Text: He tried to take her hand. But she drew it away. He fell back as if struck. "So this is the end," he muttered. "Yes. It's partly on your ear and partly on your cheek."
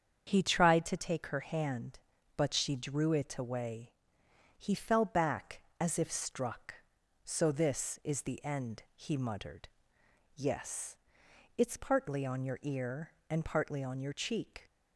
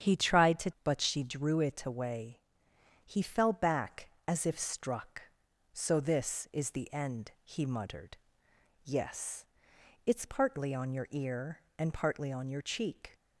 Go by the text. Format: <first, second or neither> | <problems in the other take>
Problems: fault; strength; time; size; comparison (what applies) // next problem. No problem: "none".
first | starts louder than the rest; strong; until 1.1 s; 9 dB; strong in the first // skips "take her hand"; at 0.7 s